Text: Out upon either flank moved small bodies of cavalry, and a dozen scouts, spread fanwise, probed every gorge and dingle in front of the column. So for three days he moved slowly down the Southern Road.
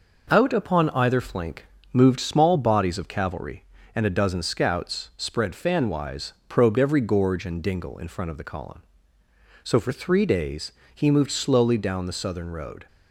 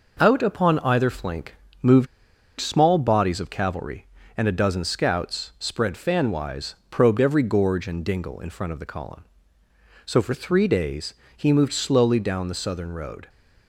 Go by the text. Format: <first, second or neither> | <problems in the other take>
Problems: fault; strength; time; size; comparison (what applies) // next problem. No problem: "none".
first | pauses between "flank" and "moved"; slight; at 1.5 s; 0.26 s long; slight in the first // pauses between "moved" and "small"; noticeable; at 2.0 s; 0.53 s long // pauses between "days" and "he"; slight; at 11.1 s; 0.20 s long; slight in the first